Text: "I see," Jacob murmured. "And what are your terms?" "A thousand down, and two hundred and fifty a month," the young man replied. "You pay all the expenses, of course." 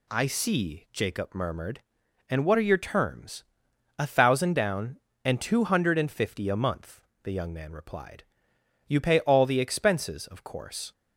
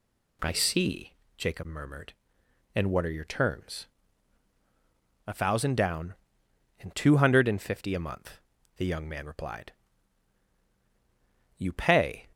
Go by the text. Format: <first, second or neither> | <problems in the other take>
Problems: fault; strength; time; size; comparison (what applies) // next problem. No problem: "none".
first | stops before "all the expenses of course"; at 12.3 s